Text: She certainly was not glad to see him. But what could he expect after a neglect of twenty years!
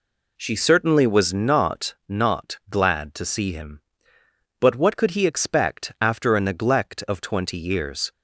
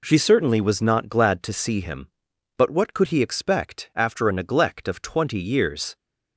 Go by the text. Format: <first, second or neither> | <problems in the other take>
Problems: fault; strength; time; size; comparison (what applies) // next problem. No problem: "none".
second | says "not" twice; at 2.0 s